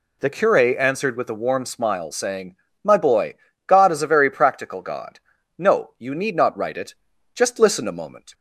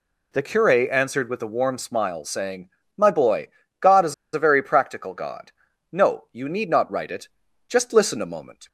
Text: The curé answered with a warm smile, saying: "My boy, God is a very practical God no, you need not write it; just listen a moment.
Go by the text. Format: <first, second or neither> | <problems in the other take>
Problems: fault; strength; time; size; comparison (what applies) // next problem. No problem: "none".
first | pauses between "is" and "a"; slight; at 4.1 s; 0.20 s long // pauses between "God" and "no"; at 5.5 s; 0.40 s long; also in the first